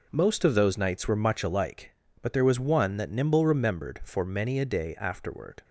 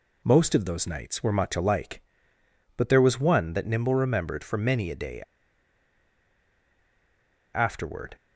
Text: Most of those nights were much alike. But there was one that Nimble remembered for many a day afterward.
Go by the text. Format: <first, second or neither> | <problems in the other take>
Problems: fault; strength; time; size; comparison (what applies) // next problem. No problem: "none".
first | pauses between "day" and "afterward"; strong; at 5.2 s; 2.3 s long